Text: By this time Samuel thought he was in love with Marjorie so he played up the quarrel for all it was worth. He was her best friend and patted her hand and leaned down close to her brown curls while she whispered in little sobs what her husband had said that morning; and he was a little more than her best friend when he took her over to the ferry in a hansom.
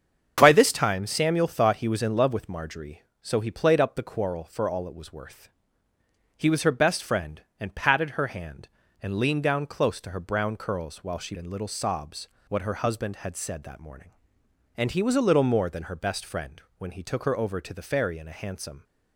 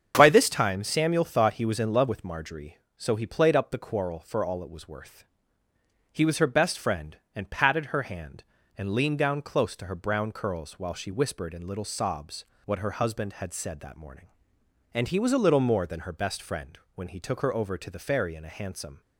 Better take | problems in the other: second | starts louder than the rest; strong; until 1.3 s; 7.5 dB; strong in the second // skips "whispered"; at 11.3 s // pauses between "sobs" and "what"; slight; at 12.2 s; 0.20 s long; slight in the second // pauses between "friend" and "when"; slight; at 16.6 s; 0.16 s long; slight in the second

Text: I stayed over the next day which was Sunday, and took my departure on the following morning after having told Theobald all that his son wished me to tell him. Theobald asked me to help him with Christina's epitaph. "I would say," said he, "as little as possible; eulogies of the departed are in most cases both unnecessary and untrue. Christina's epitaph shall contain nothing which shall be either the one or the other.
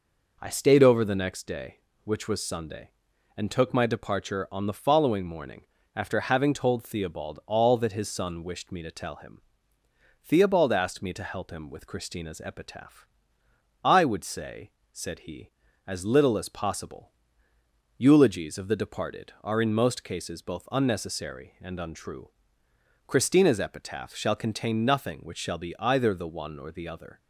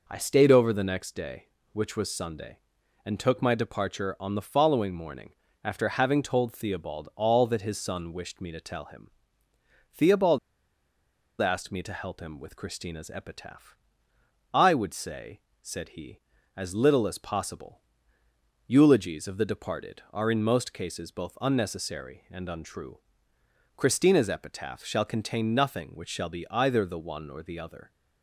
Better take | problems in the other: first | pauses between "morning" and "after"; slight; at 5.3 s; 0.30 s long; slight in the first // pauses between "Theobald" and "asked"; at 10.3 s; 1.0 s long

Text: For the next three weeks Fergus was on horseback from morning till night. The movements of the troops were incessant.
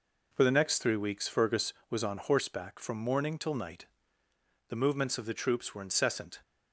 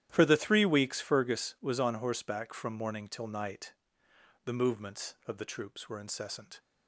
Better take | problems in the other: first | starts louder than the rest; strong; until 1.1 s; 11.5 dB // skips "next"; at 0.3 s

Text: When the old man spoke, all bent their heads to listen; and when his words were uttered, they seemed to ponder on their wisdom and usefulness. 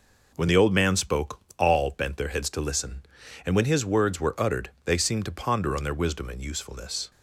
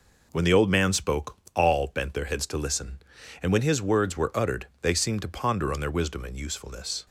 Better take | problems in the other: neither | none

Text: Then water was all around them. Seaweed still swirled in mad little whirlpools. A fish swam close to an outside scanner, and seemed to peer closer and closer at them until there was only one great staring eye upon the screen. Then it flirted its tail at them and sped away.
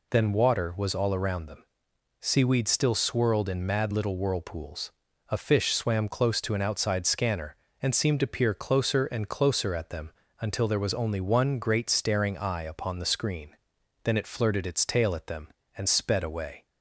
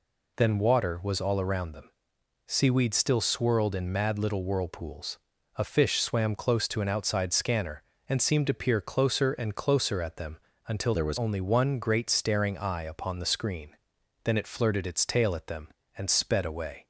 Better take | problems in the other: first | pauses between "them" and "until"; slight; at 10.3 s; 0.28 s long; slight in the first // changes voice from "there" to "was"; from 10.9 to 11.1 s; 0.2 s long

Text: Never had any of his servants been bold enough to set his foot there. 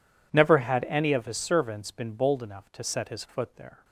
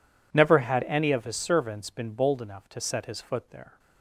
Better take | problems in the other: neither | none

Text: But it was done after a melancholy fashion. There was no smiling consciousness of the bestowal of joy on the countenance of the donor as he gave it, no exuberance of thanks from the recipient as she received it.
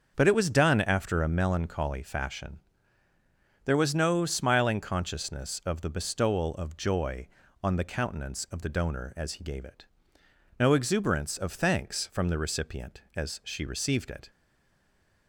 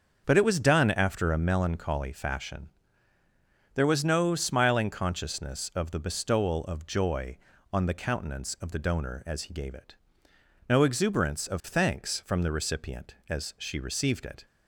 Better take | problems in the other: second | starts louder than the rest; until 1.1 s; 7 dB; also in the second // stays silent after the last word; from 14.2 s on; 1.0 s long

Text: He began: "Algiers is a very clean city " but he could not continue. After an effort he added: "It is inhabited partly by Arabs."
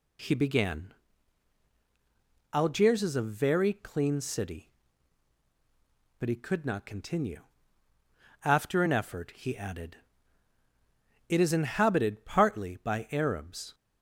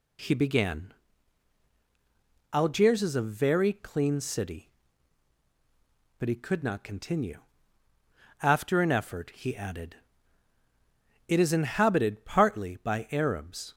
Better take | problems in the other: neither | none

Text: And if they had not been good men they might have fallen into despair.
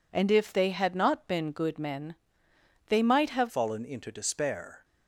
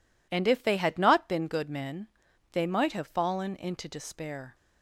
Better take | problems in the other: second | pauses between "men" and "they"; noticeable; at 2.1 s; 0.72 s long; also in the second // changes voice at "fallen"; from 3.4 s on; 1.4 s long

